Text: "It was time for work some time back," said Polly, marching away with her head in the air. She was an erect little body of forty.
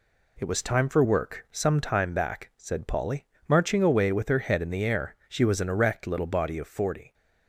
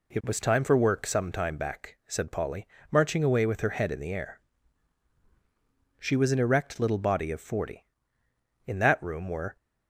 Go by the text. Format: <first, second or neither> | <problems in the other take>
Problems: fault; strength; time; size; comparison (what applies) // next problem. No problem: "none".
first | goes on to say "In that room were"; noticeable; from 8.6 s on; 0.90 s long